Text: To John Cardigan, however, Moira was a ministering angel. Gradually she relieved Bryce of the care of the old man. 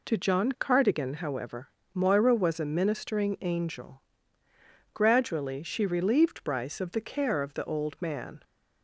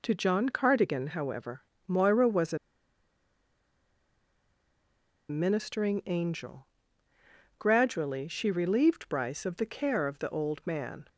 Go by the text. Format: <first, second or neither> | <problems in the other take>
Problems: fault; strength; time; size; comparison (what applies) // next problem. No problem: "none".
first | pauses between "a" and "ministering"; strong; at 2.5 s; 2.7 s long